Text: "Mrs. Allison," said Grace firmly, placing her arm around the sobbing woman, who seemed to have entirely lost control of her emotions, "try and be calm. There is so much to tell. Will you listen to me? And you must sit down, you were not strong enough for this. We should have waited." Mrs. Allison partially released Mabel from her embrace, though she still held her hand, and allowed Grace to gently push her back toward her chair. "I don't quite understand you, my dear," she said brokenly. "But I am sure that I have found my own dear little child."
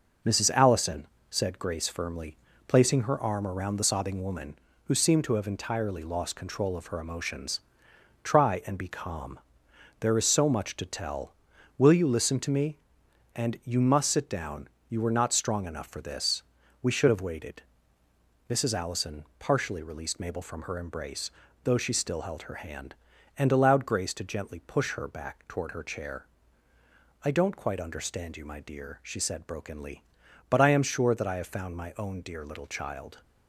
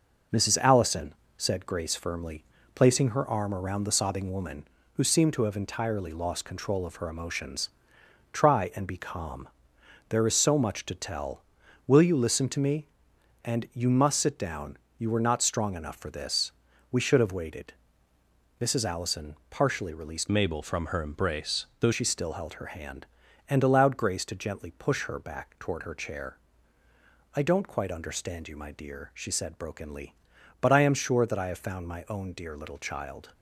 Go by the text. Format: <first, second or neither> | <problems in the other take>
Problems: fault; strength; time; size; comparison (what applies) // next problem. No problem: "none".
first | changes voice from "Mabel" to "though"; from 20.2 to 21.9 s; 1.7 s long